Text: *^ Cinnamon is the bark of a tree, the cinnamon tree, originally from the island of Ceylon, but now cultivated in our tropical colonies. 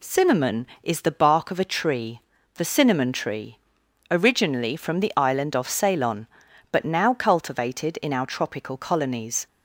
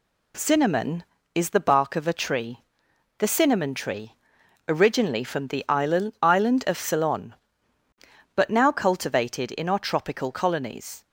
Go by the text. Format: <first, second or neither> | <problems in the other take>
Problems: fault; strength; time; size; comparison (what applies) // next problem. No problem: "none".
first | says "island" twice; at 6.2 s